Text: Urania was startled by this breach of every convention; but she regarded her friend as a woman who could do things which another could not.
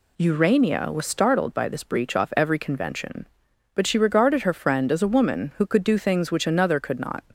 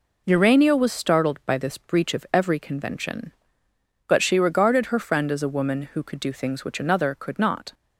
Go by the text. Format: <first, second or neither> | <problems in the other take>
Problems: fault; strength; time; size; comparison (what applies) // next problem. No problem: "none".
second | says "off" for "of"; at 2.1 s